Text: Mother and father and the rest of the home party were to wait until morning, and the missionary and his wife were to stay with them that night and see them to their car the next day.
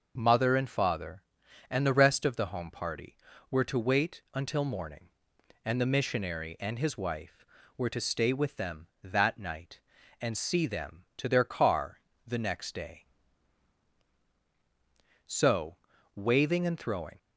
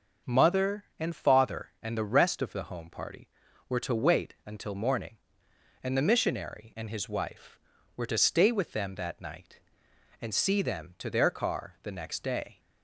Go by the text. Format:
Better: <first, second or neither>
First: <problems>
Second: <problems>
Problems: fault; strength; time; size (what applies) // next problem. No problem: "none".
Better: second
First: pauses between "car" and "the"; slight; at 11.9 s; 0.26 s long // goes on to say "So waving and throwing"; strong; from 15.2 s on; 1.9 s long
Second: none